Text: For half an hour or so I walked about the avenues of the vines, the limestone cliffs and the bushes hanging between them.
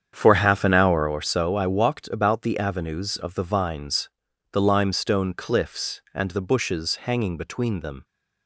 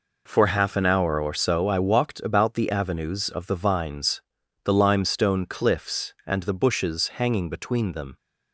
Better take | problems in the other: second | starts louder than the rest; strong; until 1.1 s; 8 dB

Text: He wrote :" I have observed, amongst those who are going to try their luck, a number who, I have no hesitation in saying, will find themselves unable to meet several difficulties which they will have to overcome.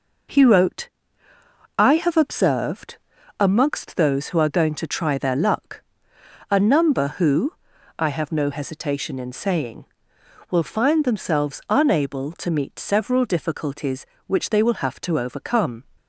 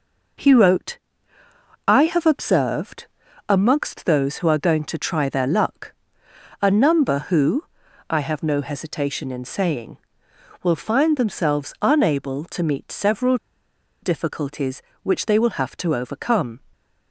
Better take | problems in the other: first | pauses between "several" and "difficulties"; noticeable; at 13.3 s; 0.65 s long

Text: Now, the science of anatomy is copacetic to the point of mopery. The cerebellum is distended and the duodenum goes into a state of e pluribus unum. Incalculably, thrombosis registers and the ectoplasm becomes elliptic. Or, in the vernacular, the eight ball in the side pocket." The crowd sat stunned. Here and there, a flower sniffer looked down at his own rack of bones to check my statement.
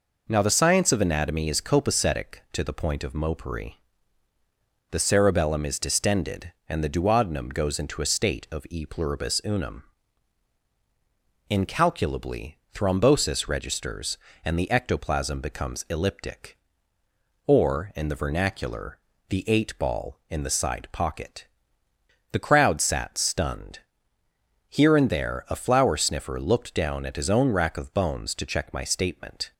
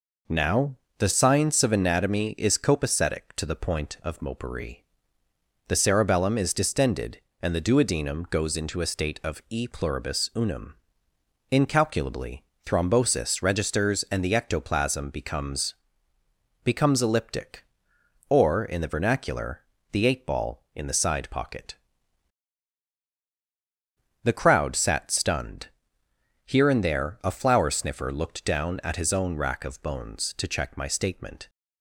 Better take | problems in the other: first | says "becomes" twice; at 16.6 s

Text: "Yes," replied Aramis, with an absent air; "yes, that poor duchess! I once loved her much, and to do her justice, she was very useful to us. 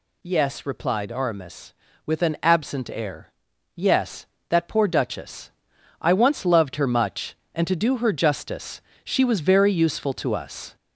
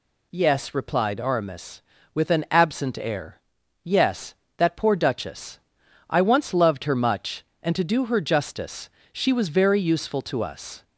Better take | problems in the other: second | gets louder; throughout; 4 dB

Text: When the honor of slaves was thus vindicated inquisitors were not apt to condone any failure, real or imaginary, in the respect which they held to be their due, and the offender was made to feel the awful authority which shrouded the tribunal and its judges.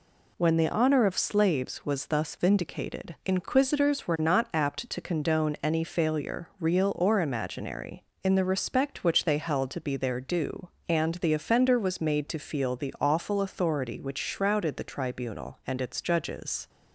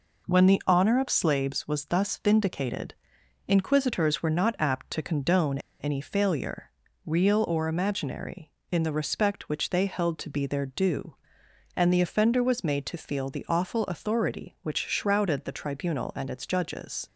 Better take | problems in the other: first | pauses between "vindicated" and "inquisitors"; noticeable; at 2.9 s; 0.52 s long // pauses between "condone" and "any"; slight; at 5.5 s; 0.21 s long

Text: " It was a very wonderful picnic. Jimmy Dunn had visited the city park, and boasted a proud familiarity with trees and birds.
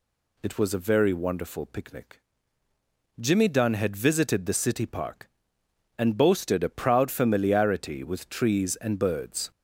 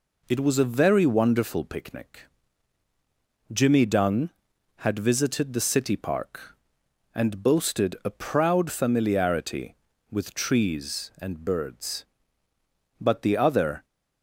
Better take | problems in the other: first | goes on to say "But the other"; noticeable; from 12.9 s on; 0.86 s long

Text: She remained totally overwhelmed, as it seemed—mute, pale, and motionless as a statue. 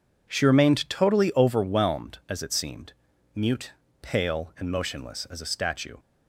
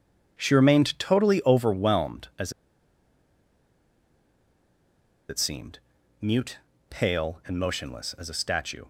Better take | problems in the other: first | pauses between "as" and "it"; strong; at 2.5 s; 2.7 s long

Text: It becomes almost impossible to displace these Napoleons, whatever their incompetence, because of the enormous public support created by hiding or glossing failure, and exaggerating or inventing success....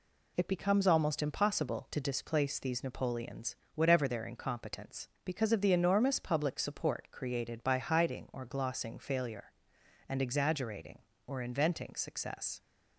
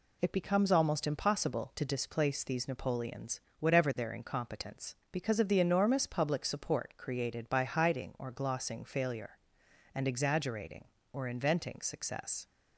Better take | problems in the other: neither | none

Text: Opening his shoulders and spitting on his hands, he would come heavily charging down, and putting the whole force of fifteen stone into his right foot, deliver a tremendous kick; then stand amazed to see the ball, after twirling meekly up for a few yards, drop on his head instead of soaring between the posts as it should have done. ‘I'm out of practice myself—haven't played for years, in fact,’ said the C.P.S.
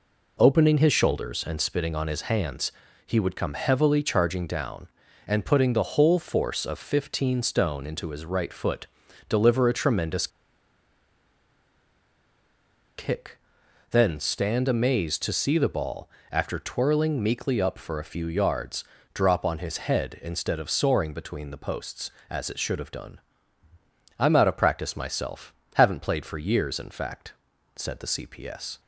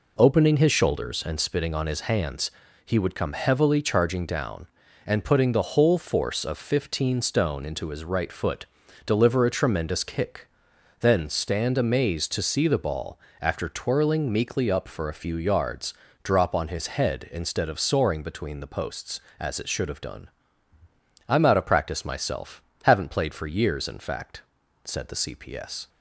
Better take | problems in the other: second | pauses between "tremendous" and "kick"; strong; at 10.2 s; 2.6 s long

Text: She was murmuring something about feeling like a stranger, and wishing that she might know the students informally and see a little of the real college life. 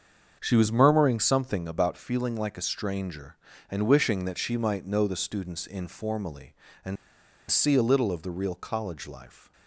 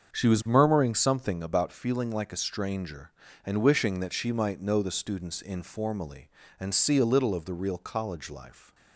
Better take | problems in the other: second | starts louder than the rest; until 1.4 s; 7 dB; also in the second // pauses between "and" and "see"; noticeable; at 6.9 s; 0.54 s long

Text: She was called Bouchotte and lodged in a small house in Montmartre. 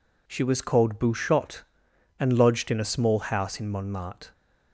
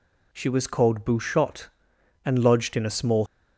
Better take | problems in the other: first | stops before "house in Montmartre"; at 3.2 s

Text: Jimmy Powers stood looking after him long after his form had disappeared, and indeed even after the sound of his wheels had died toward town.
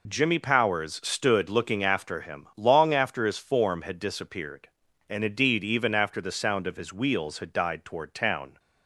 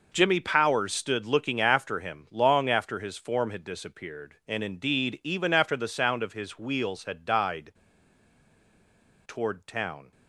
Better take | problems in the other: first | pauses between "died" and "toward"; strong; at 7.7 s; 1.5 s long

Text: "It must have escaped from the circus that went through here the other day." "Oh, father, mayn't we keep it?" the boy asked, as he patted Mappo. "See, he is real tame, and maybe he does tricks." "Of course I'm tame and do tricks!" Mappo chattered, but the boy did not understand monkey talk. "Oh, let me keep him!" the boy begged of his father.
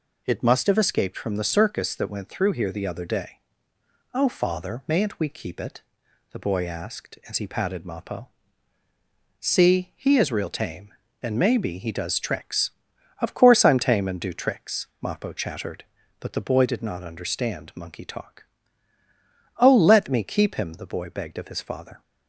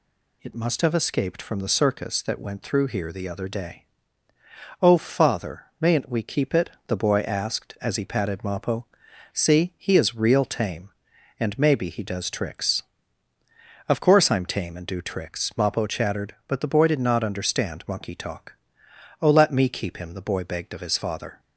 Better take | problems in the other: neither | none

